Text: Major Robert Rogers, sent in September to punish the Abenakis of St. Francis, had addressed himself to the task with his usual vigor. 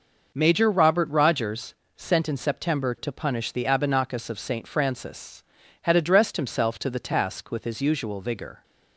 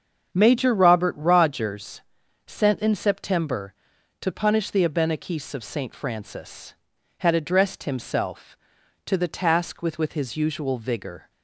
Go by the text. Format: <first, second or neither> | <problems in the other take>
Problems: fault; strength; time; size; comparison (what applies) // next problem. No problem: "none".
first | starts louder than the rest; strong; until 1.3 s; 7.5 dB // says "with" twice; at 9.9 s